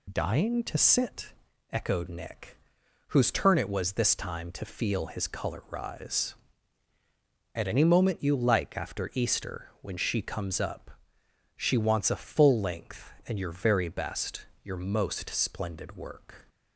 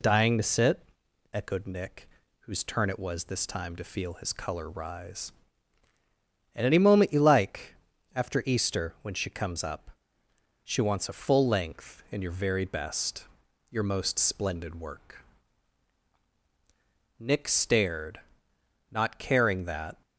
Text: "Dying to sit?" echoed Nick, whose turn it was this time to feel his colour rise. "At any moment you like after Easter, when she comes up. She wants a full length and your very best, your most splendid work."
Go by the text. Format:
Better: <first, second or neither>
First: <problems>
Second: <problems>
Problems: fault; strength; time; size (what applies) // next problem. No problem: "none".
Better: first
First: none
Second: pauses between "like" and "after"; at 7.7 s; 0.40 s long // goes on to say "Nick stared not caring that"; strong; from 17.1 s on; 2.8 s long